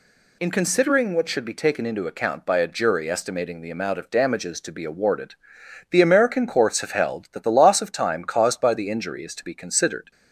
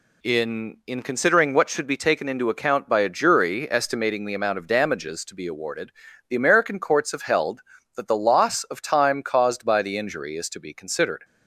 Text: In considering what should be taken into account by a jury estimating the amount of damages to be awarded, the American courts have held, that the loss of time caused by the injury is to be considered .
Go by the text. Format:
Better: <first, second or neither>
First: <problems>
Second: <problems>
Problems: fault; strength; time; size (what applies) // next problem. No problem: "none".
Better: first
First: none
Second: says "In" twice; at 0.8 s